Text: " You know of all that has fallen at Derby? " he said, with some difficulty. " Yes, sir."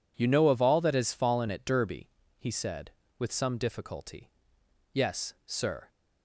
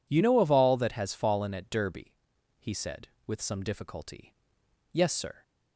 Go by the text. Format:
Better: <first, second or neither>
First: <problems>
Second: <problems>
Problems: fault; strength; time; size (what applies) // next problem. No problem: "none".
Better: neither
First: none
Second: none